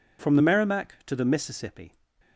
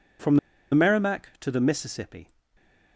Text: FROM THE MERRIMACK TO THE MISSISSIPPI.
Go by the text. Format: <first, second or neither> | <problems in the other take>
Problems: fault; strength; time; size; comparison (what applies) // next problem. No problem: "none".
first | pauses between "FROM" and "THE"; slight; at 0.3 s; 0.35 s long